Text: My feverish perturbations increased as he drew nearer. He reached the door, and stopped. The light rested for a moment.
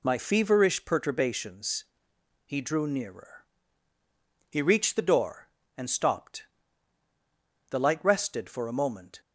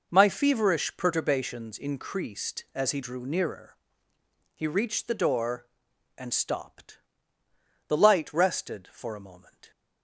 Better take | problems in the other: second | skips "increased as"; at 2.1 s

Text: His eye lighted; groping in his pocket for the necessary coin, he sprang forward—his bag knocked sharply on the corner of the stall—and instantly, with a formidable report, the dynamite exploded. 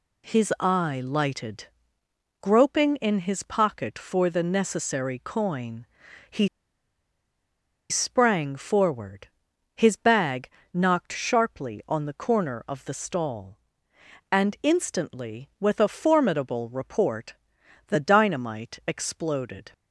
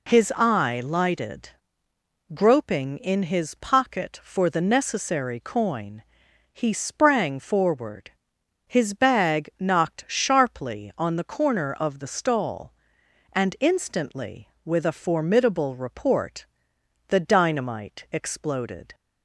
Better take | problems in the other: second | pauses between "he" and "sprang"; strong; at 6.4 s; 1.4 s long // pauses between "bag" and "knocked"; slight; at 10.4 s; 0.24 s long

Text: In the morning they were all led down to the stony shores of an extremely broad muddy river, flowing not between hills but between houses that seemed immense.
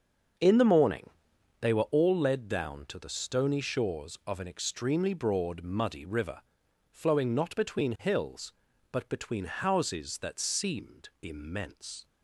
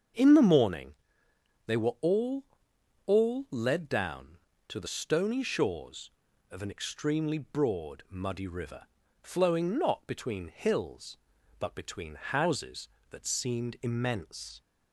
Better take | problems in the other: first | starts louder than the rest; until 1.8 s; 7 dB; also in the first // pauses between "morning" and "they"; noticeable; at 0.9 s; 0.72 s long; noticeable in the first // says "all" twice; at 3.0 s

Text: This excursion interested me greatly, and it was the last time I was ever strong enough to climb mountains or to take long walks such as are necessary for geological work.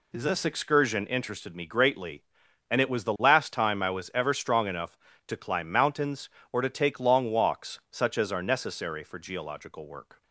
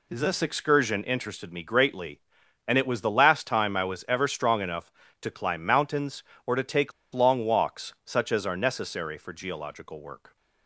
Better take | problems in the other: first | pauses between "take" and "long"; slight; at 6.9 s; 0.21 s long

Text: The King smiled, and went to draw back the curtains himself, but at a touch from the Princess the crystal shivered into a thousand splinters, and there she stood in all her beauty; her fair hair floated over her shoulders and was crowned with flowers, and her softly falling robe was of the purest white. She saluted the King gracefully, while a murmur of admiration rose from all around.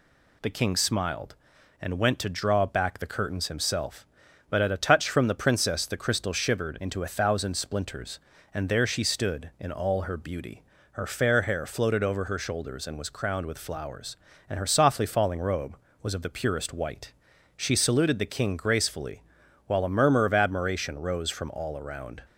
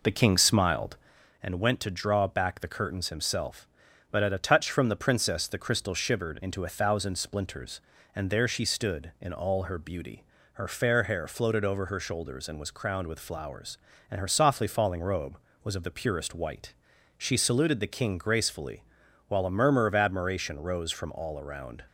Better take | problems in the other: first | starts louder than the rest; noticeable; until 1.3 s; 4 dB

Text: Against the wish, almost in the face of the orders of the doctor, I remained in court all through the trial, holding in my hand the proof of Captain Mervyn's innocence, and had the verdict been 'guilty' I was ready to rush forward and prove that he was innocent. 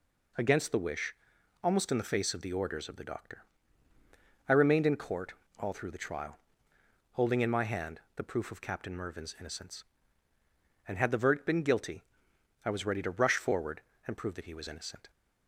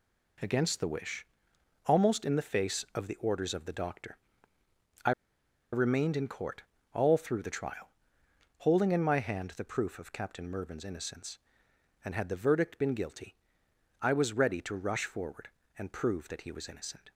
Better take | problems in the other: first | pauses between "I" and "remained"; noticeable; at 5.1 s; 0.61 s long // pauses between "court" and "all"; slight; at 6.6 s; 0.30 s long; slight in the first // pauses between "guilty" and "I"; noticeable; at 13.3 s; 0.66 s long; noticeable in the first

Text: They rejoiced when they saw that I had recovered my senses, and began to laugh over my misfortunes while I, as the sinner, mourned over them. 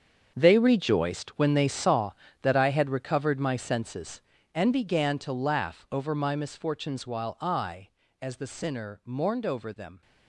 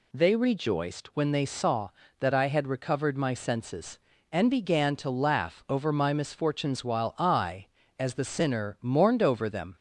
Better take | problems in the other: second | gets quieter; strong; throughout; 12.5 dB

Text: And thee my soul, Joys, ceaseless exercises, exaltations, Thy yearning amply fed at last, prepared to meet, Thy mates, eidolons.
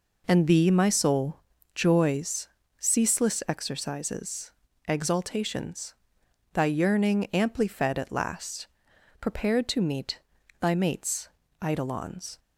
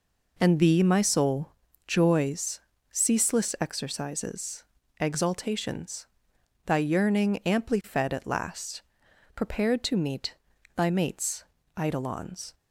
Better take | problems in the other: neither | none

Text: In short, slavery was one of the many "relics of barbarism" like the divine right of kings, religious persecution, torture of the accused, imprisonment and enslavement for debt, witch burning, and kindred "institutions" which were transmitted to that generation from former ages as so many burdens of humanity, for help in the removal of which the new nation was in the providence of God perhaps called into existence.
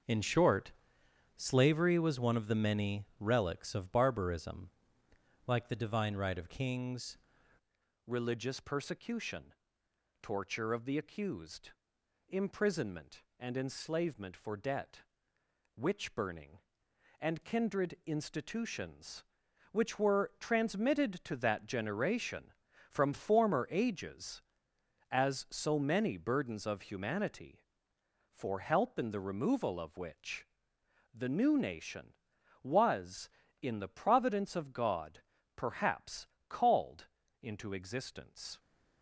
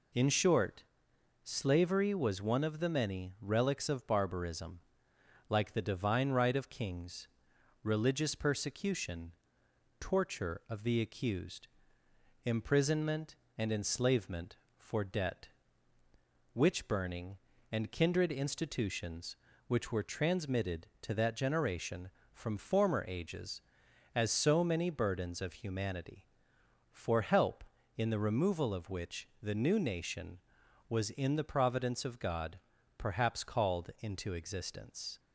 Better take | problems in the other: second | starts louder than the rest; until 1.7 s; 6.5 dB // pauses between "barbarism" and "like"; noticeable; at 4.6 s; 0.78 s long; noticeable in the second // changes voice at "religious"; from 8.0 s on; 30.5 s long // pauses between "which" and "the"; noticeable; at 30.4 s; 0.68 s long; slight in the second // pauses between "God" and "perhaps"; slight; at 35.2 s; 0.34 s long; also in the second // pauses between "perhaps" and "called"; slight; at 36.2 s; 0.22 s long // pauses between "called" and "into"; slight; at 37.0 s; 0.34 s long

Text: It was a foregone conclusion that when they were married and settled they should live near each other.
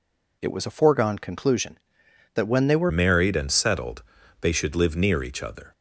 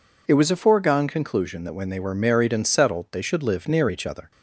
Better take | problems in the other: second | changes voice at "married"; from 2.8 s on; 2.9 s long // pauses between "settled" and "they"; at 4.0 s; 0.38 s long

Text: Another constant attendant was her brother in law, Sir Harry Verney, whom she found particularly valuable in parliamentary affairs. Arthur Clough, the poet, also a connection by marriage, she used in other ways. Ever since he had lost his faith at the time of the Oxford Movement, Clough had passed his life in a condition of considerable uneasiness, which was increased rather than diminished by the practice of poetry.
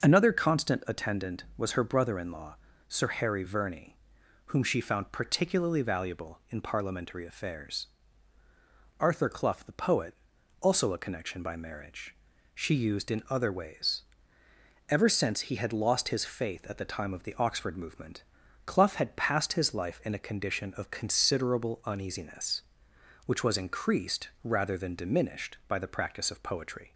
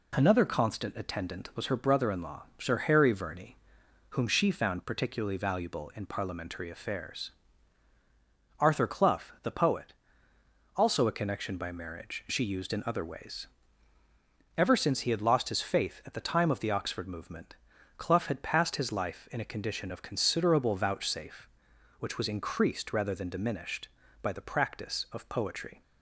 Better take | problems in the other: first | says "vouchsafe" for "uneasiness"; at 20.7 s

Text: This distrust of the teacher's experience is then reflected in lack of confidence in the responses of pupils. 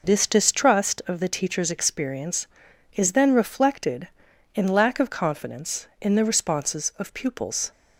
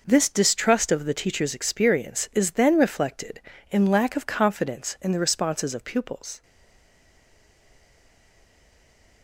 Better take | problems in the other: first | stays silent after the last word; strong; from 6.4 s on; 2.8 s long

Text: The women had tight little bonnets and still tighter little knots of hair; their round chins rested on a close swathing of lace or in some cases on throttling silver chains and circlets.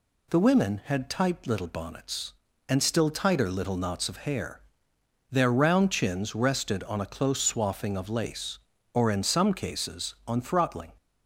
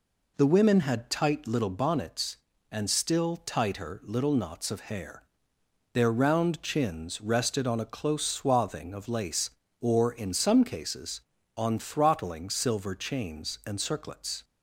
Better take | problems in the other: second | stops before "silver chains and circlets"; at 10.9 s

